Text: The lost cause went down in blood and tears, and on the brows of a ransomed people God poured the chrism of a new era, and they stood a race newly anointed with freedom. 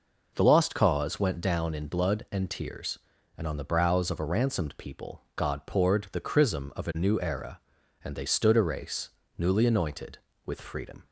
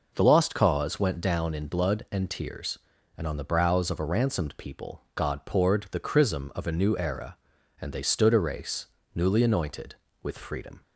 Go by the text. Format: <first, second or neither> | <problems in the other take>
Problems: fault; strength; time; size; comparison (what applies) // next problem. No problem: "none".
neither | pauses between "race" and "newly"; slight; the same in both